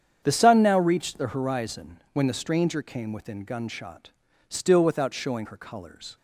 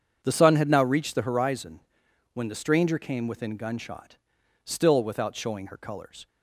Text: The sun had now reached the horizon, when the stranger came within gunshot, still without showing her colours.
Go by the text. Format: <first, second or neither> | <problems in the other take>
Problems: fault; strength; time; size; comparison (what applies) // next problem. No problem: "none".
second | starts louder than the rest; strong; until 1.2 s; 8.5 dB; strong in the second // skips "had"; at 0.6 s